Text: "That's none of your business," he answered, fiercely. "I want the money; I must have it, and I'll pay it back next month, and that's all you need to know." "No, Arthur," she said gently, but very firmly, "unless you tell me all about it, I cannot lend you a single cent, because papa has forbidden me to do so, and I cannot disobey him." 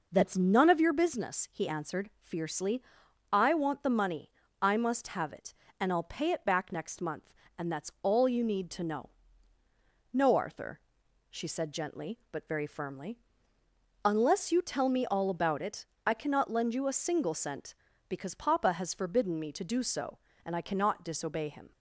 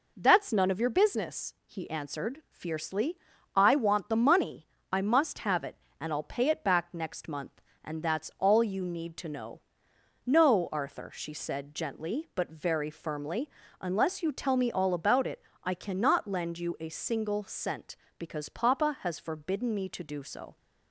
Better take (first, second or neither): first